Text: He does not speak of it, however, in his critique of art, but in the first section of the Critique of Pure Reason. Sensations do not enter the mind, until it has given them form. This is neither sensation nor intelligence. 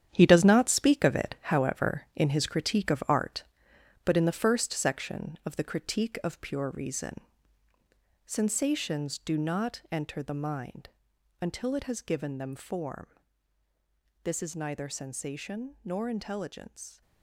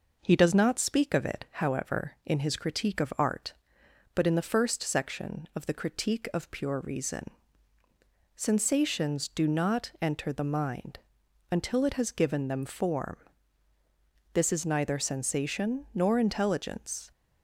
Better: second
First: gets quieter; strong; throughout; 10 dB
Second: none

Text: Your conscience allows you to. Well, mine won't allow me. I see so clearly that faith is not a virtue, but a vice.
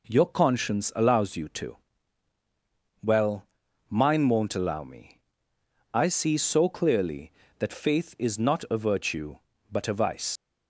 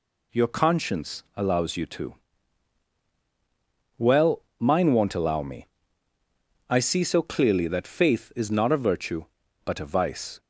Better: second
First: leaves "vice" unfinished; at 10.3 s; 80 ms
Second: none

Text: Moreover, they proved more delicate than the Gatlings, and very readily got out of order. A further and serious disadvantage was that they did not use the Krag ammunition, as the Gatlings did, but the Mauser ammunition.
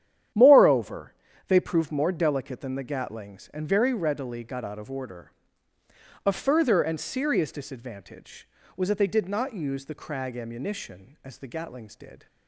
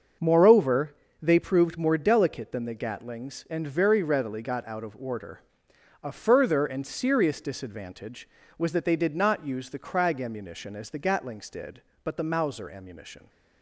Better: second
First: starts louder than the rest; strong; until 1.7 s; 10 dB // stops before "but the Mauser ammunition"; at 12.2 s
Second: starts louder than the rest; until 1.4 s; 6.5 dB

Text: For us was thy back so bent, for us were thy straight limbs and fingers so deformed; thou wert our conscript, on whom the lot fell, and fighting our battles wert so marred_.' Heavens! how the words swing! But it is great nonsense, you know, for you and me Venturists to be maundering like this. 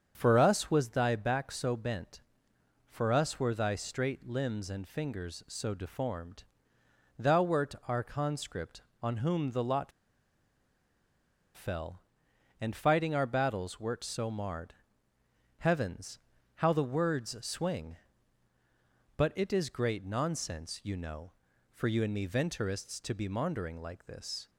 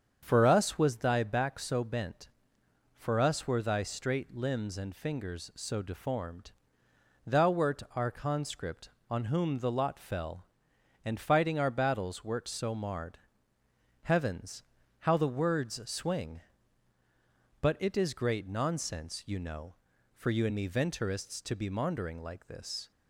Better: second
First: starts louder than the rest; strong; until 1.1 s; 7.5 dB // pauses between "lot" and "fell"; strong; at 9.9 s; 1.6 s long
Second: starts louder than the rest; strong; until 1.2 s; 7.5 dB

